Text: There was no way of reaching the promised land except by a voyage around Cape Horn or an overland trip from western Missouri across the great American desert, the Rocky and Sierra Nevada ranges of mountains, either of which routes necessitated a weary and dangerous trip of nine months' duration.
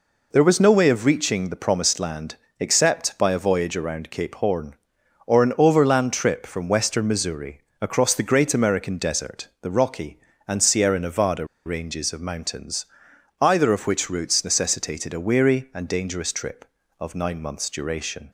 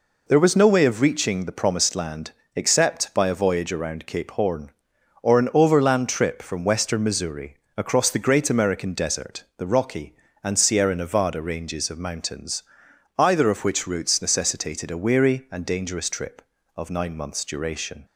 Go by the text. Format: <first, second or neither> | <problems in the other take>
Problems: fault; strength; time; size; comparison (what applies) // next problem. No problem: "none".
second | pauses between "land" and "except"; slight; at 2.3 s; 0.22 s long; slight in the second // pauses between "Missouri" and "across"; slight; at 7.5 s; 0.22 s long; slight in the second // pauses between "Nevada" and "ranges"; slight; at 11.4 s; 0.20 s long